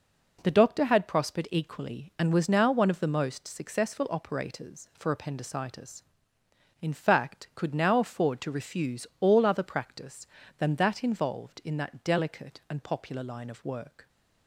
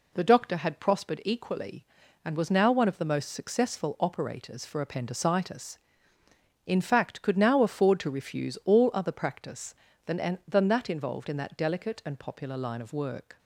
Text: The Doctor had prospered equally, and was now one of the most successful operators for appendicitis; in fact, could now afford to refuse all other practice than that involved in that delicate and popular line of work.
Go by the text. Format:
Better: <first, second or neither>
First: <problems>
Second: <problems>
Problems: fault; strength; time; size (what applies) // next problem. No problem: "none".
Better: first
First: none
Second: says "than" twice; at 10.4 s